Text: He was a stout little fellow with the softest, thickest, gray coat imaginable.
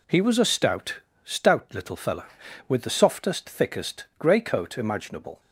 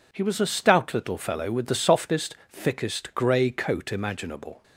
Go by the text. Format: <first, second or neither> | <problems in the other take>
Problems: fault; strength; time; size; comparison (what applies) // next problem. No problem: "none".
second | says "stout" twice; at 1.2 s